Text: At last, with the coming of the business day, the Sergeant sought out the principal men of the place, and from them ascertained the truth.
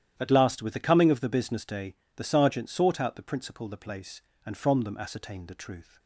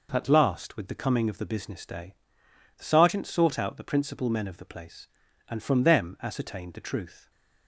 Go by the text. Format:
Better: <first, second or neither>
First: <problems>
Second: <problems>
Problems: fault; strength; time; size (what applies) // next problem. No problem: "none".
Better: second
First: starts louder than the rest; strong; until 1.1 s; 11 dB // skips "men of"; at 3.6 s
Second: none